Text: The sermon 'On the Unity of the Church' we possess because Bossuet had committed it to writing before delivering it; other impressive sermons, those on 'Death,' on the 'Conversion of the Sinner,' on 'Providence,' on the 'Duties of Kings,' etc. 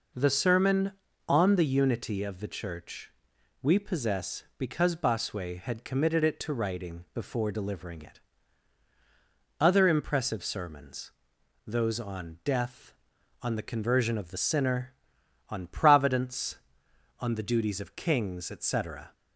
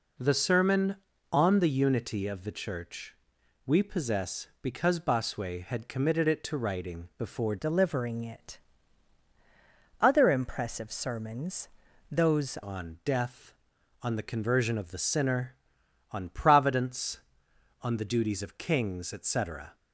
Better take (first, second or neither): first